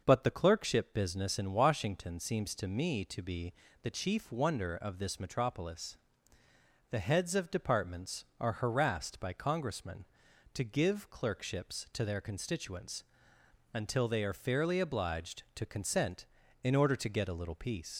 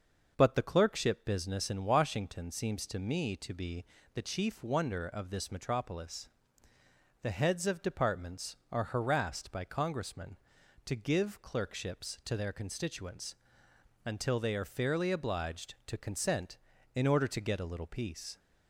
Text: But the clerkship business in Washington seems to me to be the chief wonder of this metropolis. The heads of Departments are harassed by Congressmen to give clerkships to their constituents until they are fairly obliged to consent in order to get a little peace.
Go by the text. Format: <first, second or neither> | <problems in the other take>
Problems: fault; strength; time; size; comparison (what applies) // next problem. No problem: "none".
second | starts louder than the rest; until 1.0 s; 6 dB; also in the second // pauses between "be" and "the"; slight; at 3.5 s; 0.30 s long; slight in the second // pauses between "constituents" and "until"; noticeable; at 13.0 s; 0.70 s long; noticeable in the second // leaves "peace" unfinished; at 17.9 s; 75 ms